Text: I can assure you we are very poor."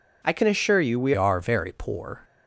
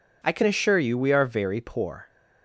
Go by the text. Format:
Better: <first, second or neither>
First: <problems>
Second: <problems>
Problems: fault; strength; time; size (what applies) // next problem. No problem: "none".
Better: second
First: changes voice at "are"; from 1.1 s on; 1.1 s long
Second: none